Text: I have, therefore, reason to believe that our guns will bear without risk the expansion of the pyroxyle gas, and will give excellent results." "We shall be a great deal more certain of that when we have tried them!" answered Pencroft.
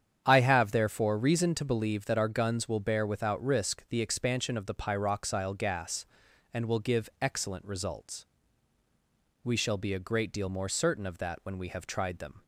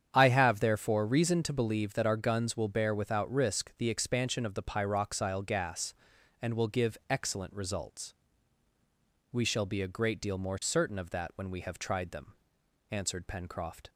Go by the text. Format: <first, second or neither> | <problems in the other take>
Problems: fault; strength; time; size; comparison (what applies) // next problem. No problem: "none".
second | starts louder than the rest; strong; until 1.2 s; 8.5 dB; strong in the second // stops before "answered Pencroft"; at 12.4 s